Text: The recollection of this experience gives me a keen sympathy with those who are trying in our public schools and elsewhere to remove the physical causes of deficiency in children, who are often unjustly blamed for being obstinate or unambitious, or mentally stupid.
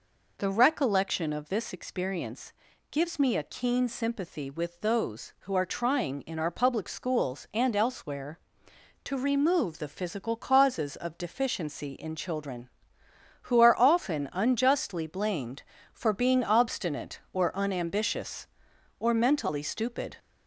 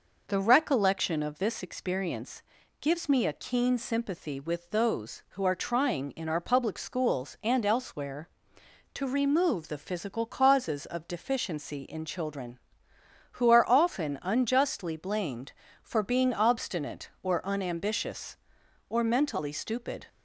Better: second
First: gets louder; slight; throughout; 3 dB // pauses between "experience" and "gives"; at 2.5 s; 0.40 s long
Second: pauses between "experience" and "gives"; at 2.4 s; 0.40 s long

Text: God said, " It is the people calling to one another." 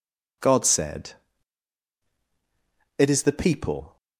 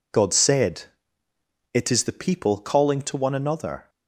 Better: second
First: stops before "calling to one another"; at 3.9 s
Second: none

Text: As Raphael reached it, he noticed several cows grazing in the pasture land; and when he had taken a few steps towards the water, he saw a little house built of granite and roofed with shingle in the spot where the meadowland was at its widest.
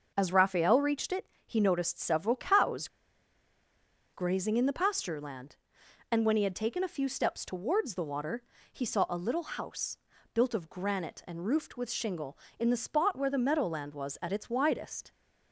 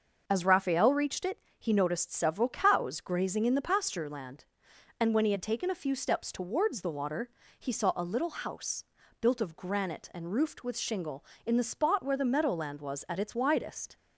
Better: second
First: starts louder than the rest; until 1.1 s; 6 dB // pauses between "cows" and "grazing"; strong; at 2.8 s; 1.2 s long // pauses between "house" and "built"; slight; at 9.9 s; 0.34 s long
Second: starts louder than the rest; until 1.2 s; 6 dB // pauses between "house" and "built"; slight; at 8.8 s; 0.34 s long

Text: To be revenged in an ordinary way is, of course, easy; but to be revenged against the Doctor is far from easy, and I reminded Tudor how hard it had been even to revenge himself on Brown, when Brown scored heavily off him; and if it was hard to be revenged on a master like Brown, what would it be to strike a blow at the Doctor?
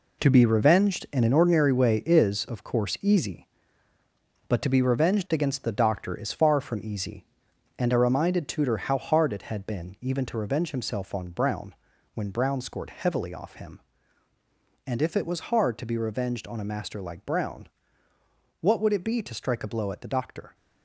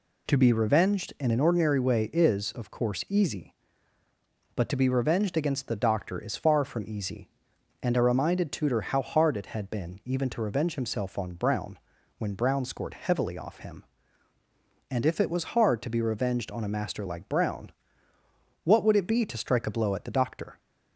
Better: second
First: gets quieter; strong; throughout; 9 dB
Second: none

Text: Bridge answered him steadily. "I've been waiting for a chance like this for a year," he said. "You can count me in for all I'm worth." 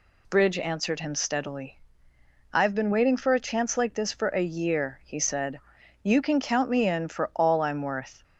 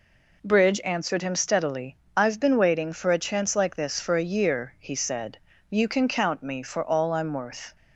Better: first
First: none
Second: skips "in"; at 6.6 s

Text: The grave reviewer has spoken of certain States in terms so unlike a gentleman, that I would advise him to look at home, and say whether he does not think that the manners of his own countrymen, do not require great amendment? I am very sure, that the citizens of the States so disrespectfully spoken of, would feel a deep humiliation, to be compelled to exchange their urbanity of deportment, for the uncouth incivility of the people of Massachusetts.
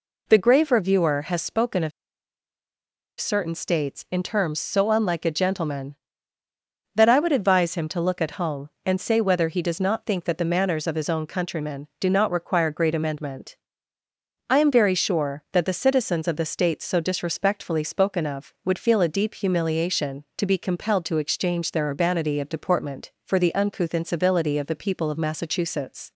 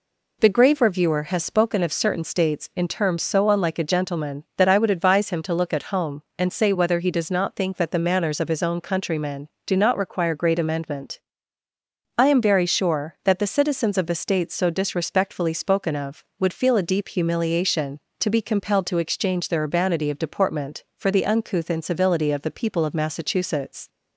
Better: second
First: pauses between "of" and "certain"; strong; at 1.9 s; 1.2 s long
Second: none

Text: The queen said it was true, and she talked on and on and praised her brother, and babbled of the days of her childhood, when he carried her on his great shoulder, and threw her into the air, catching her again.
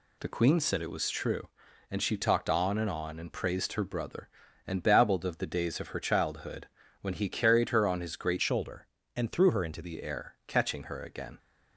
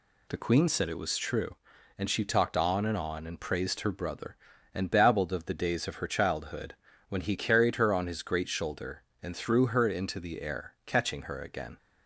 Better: second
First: changes voice from "shoulder" to "into"; from 8.4 to 9.8 s; 1.4 s long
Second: none

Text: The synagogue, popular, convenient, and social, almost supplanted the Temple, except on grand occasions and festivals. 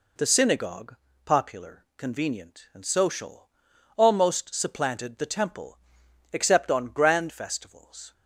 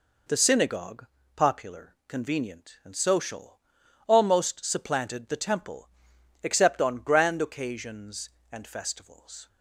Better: second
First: skips "occasions and"; at 7.3 s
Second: none

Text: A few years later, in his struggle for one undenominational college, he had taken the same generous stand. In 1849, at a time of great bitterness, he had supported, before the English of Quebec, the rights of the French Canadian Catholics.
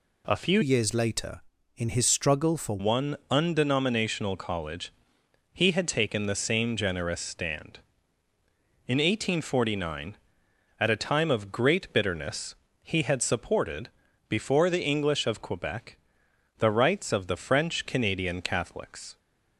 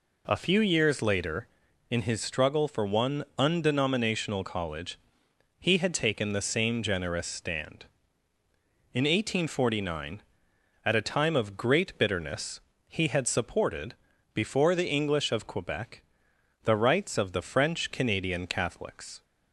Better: second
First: changes voice from "years" to "for"; from 0.6 to 2.7 s; 2.1 s long // pauses between "one" and "undenominational"; slight; at 3.1 s; 0.16 s long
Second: pauses between "one" and "undenominational"; slight; at 3.2 s; 0.16 s long

